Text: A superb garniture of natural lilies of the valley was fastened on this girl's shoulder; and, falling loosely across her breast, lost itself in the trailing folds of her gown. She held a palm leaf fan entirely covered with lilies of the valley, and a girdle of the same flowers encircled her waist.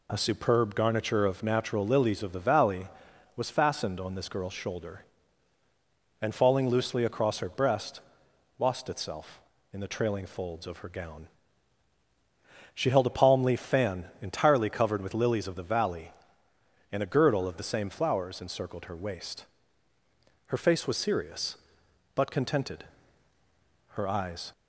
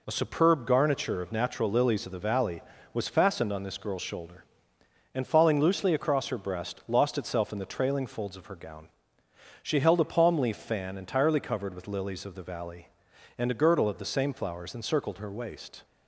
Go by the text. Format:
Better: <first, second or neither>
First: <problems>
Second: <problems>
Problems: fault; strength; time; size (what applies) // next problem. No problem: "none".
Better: second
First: goes on to say "Her face was serious but contented her eyes"; strong; from 20.4 s on; 4.0 s long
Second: none